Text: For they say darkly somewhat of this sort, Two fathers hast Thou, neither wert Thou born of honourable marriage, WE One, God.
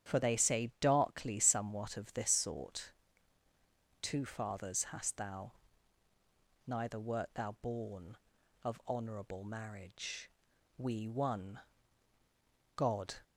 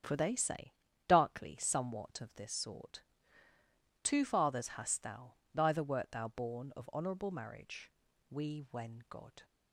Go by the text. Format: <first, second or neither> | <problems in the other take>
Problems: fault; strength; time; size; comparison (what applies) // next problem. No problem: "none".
first | starts louder than the rest; strong; until 1.3 s; 9 dB; strong in the first // pauses between "say" and "darkly"; slight; at 0.7 s; 0.34 s long // says "When" for "One"; at 8.7 s